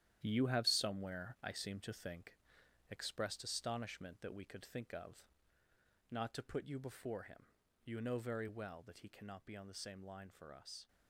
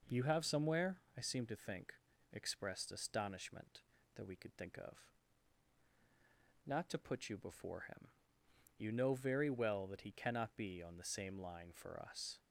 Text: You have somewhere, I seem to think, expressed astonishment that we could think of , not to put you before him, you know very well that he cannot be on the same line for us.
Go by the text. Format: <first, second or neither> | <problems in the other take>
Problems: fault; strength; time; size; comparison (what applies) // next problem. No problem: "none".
second | gets quieter; strong; throughout; 9.5 dB